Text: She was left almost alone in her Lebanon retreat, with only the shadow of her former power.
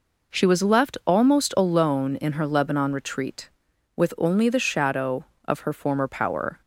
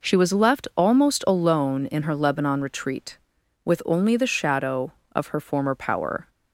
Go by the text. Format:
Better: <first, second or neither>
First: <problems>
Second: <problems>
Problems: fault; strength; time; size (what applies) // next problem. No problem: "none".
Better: neither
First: none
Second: none